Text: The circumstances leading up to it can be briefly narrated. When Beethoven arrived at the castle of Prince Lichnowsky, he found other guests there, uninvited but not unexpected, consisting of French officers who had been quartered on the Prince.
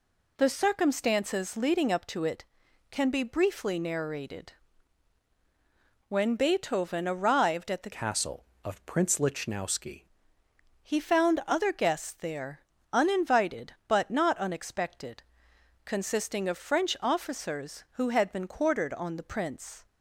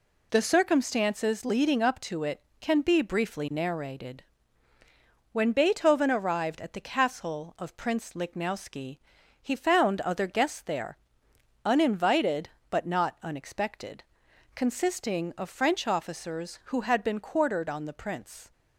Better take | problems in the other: second | changes voice from "castle" to "Lichnowsky"; from 7.9 to 10.0 s; 2.1 s long

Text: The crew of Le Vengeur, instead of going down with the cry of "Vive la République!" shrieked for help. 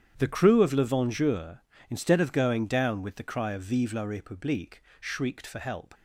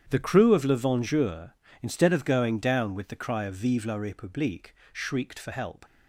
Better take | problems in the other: neither | starts louder than the rest; strong; the same in both

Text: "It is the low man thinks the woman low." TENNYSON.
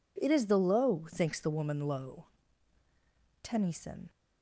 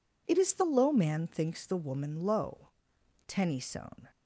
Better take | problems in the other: second | skips "man"; at 1.0 s

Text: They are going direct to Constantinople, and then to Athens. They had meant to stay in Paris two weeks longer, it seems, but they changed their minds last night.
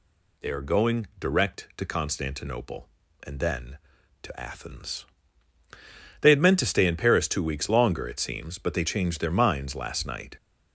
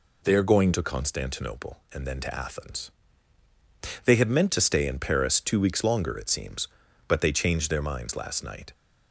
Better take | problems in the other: first | skips "direct"; at 0.7 s

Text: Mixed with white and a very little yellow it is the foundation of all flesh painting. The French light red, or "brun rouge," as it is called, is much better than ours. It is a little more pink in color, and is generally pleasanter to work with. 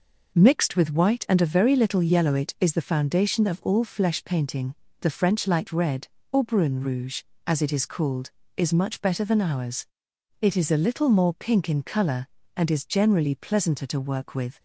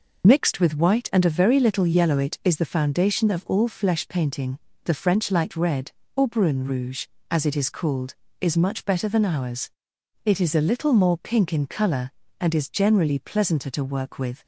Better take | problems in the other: first | loses the start of "Mixed"; at 0.2 s; 60 ms

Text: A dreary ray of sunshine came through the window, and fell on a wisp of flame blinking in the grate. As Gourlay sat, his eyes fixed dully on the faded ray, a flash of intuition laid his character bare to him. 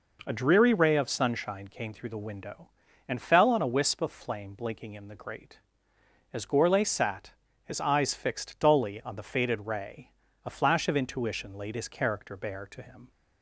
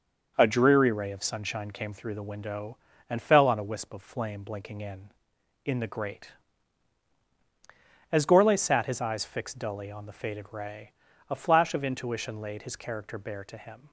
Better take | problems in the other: first | says "in" twice; at 5.6 s

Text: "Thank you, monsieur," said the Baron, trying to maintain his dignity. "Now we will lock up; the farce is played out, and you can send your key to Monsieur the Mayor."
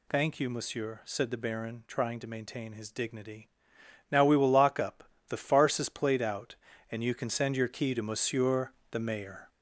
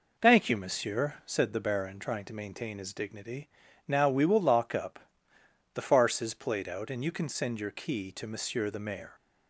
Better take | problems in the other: second | gets louder; noticeable; throughout; 5 dB // pauses between "Monsieur" and "the"; slight; at 8.7 s; 0.20 s long

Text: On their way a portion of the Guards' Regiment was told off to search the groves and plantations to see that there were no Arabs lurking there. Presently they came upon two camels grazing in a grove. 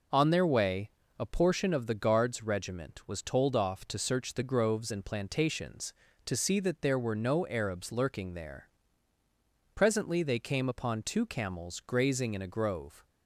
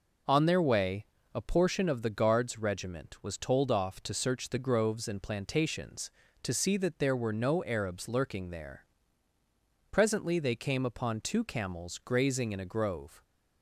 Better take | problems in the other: neither | pauses between "way" and "a"; slight; the same in both

